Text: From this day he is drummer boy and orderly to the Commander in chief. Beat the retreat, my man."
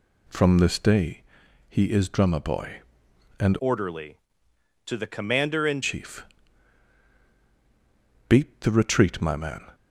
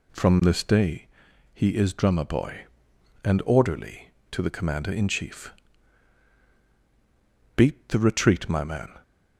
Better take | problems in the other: second | pauses between "day" and "he"; noticeable; at 1.2 s; 0.48 s long; noticeable in the second // changes voice from "orderly" to "in"; from 3.5 to 5.8 s; 2.3 s long

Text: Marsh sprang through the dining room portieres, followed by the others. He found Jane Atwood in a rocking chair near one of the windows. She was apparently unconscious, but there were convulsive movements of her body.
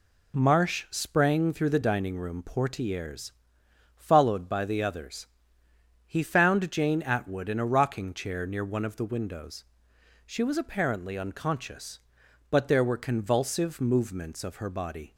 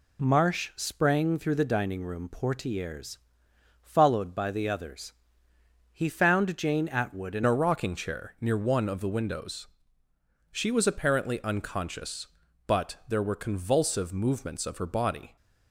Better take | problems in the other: first | changes voice at "a"; from 7.4 s on; 7.9 s long

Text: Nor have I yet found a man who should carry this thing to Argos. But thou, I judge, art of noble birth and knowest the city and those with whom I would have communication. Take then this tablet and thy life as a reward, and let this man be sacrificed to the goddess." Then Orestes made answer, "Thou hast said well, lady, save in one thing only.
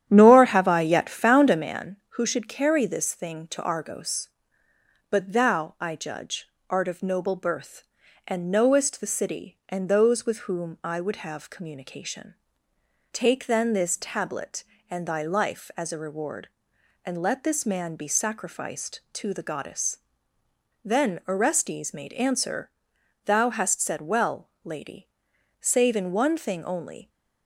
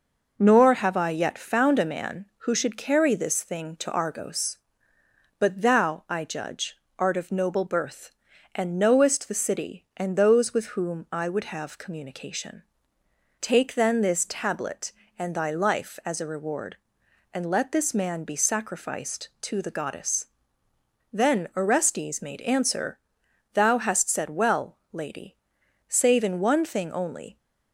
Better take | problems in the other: second | starts louder than the rest; strong; until 1.8 s; 10.5 dB

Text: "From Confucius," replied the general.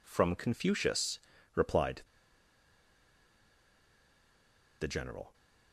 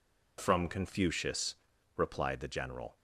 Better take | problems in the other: second | pauses between "replied" and "the"; strong; at 2.0 s; 2.7 s long

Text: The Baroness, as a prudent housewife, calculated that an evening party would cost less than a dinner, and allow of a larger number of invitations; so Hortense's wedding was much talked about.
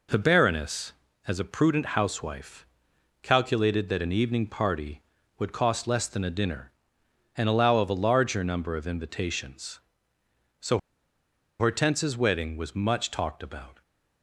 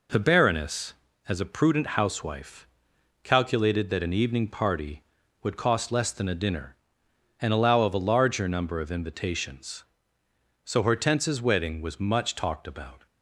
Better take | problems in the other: second | pauses between "so" and "Hortense's"; noticeable; at 10.7 s; 0.80 s long

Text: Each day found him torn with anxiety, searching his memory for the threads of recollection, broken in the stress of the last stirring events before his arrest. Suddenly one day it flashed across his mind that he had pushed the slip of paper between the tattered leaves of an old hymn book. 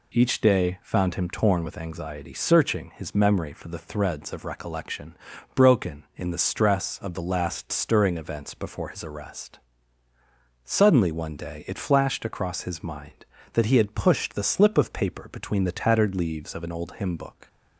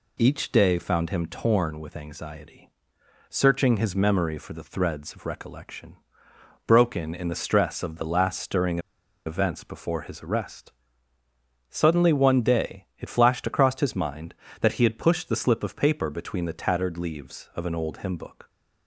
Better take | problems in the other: first | pauses between "stirring" and "events"; noticeable; at 8.7 s; 0.46 s long

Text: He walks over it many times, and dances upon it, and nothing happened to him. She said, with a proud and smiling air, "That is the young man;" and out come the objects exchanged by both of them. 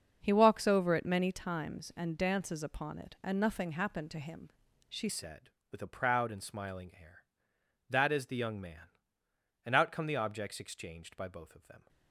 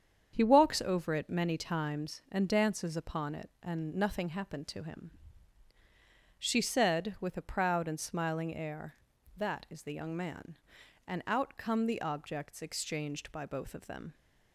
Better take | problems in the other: second | starts louder than the rest; until 1.2 s; 6.5 dB; strong in the second // changes voice at "said"; from 5.0 s on; 6.8 s long

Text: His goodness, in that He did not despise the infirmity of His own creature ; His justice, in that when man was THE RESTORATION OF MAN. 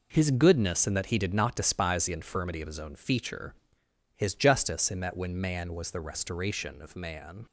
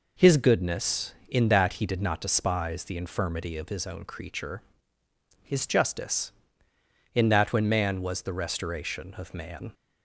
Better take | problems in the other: second | says "feature" for "creature"; at 2.9 s

